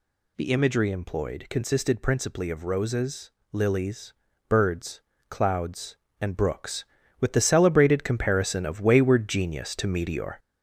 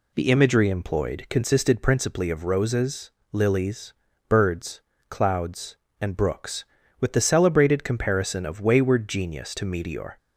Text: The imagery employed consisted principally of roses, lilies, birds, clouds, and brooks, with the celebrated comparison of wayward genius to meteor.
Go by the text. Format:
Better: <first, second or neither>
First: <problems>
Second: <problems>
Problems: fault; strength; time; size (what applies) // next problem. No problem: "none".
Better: second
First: gets louder; noticeable; throughout; 4.5 dB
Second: none